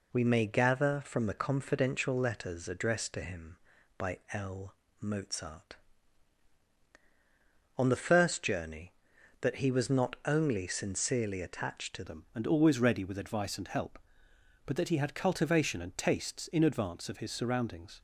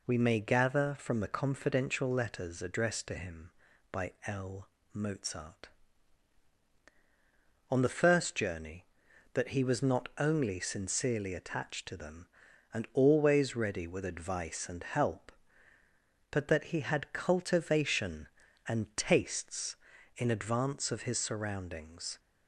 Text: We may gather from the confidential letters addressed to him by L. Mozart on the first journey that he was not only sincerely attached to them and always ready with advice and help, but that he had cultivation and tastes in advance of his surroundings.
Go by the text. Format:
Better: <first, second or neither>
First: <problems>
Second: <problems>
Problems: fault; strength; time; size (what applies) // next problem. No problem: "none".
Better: second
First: changes voice at "them"; from 12.0 s on; 6.0 s long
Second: none